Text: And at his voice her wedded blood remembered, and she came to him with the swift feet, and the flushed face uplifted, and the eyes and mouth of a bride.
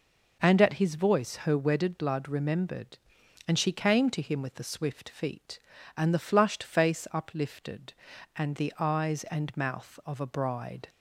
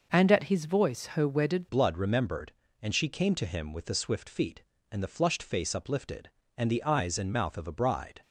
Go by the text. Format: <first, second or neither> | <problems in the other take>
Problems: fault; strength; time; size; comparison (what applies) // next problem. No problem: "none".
first | changes voice at "blood"; from 1.6 s on; 6.6 s long